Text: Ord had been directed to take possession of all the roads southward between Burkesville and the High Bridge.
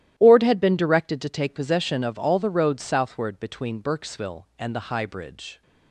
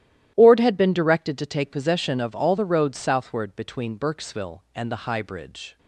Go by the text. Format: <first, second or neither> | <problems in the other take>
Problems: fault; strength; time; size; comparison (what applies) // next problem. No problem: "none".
neither | starts louder than the rest; strong; the same in both